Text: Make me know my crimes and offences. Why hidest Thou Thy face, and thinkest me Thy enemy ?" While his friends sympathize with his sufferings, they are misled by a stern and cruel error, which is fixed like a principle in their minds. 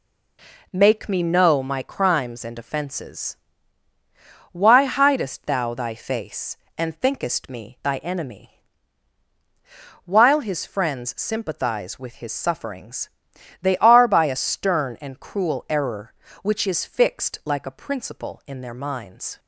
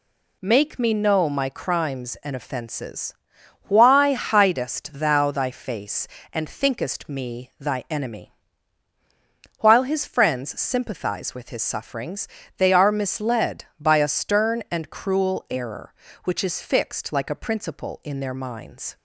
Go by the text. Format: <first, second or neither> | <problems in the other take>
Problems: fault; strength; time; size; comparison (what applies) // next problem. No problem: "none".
second | skips "misled"; at 14.0 s